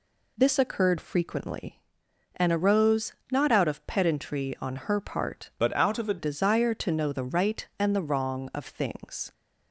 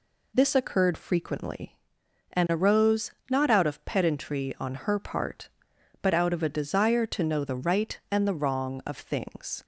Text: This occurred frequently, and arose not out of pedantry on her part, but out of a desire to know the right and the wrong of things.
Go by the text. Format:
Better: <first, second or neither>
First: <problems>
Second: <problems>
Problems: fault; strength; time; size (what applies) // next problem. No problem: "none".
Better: second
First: pauses between "arose" and "not"; slight; at 3.1 s; 0.20 s long // changes voice from "but" to "a"; from 5.5 to 6.1 s; 0.6 s long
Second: pauses between "arose" and "not"; slight; at 3.1 s; 0.20 s long